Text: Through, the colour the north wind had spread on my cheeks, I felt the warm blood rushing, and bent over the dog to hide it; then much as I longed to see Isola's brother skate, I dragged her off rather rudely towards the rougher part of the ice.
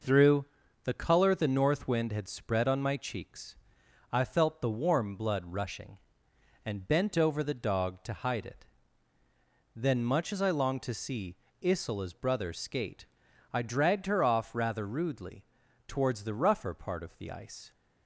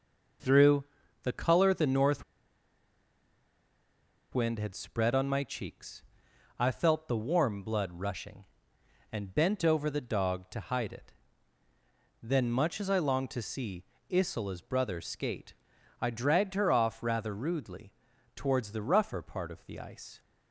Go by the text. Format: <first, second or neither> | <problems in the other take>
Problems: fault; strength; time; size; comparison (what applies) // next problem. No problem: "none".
first | pauses between "north" and "wind"; strong; at 2.2 s; 2.0 s long // pauses between "see" and "Isola's"; slight; at 13.8 s; 0.26 s long; slight in the first // pauses between "rudely" and "towards"; at 17.9 s; 0.44 s long; also in the first